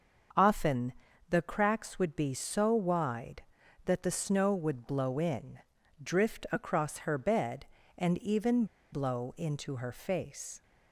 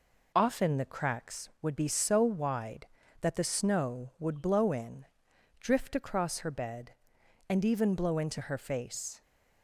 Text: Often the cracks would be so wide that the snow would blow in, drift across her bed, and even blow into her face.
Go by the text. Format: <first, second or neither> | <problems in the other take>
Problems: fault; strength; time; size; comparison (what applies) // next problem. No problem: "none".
second | starts louder than the rest; until 1.7 s; 6.5 dB // pauses between "Often" and "the"; slight; at 0.9 s; 0.36 s long // pauses between "even" and "blow"; slight; at 8.6 s; 0.26 s long